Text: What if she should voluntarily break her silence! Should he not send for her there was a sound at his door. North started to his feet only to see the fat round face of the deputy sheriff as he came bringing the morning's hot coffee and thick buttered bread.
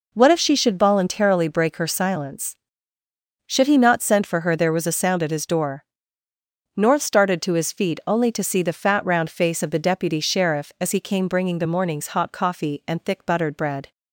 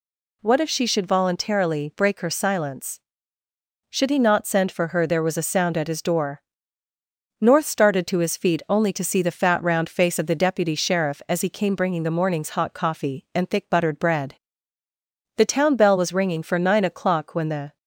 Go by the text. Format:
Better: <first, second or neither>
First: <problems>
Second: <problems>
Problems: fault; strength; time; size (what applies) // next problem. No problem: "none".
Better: first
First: none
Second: goes on to say "The town bell was ringing for nine o'clock when the"; strong; from 15.3 s on; 2.4 s long